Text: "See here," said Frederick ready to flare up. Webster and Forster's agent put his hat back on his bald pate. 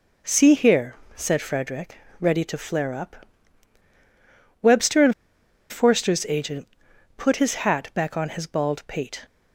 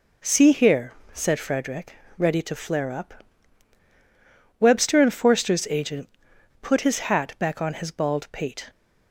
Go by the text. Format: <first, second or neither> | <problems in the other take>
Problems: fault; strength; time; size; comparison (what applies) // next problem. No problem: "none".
second | pauses between "Frederick" and "ready"; slight; at 1.9 s; 0.24 s long; slight in the second // pauses between "and" and "Forster's"; noticeable; at 5.1 s; 0.57 s long // pauses between "agent" and "put"; noticeable; at 6.6 s; 0.48 s long; noticeable in the second